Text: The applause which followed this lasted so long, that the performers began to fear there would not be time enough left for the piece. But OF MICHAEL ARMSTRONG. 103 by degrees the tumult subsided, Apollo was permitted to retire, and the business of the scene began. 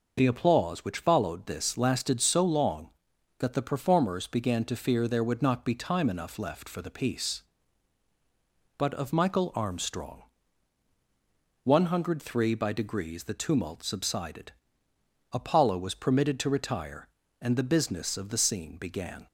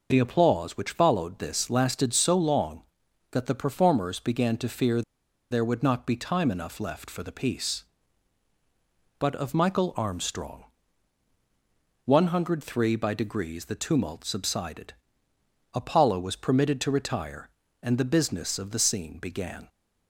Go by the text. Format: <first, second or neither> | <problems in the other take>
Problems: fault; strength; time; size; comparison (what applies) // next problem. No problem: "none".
first | pauses between "fear" and "there"; noticeable; at 5.0 s; 0.49 s long